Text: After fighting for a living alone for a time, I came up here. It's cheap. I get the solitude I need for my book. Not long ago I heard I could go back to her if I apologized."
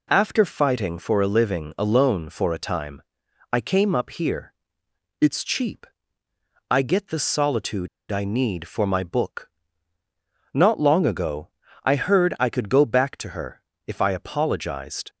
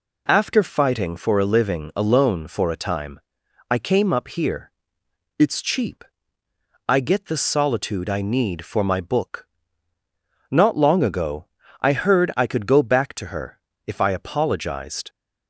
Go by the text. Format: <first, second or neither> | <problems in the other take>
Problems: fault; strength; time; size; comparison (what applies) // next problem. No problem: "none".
second | pauses between "solitude" and "I"; slight; at 7.8 s; 0.23 s long // pauses between "ago" and "I"; slight; at 11.4 s; 0.36 s long; slight in the second // pauses between "her" and "if"; slight; at 13.6 s; 0.26 s long; slight in the second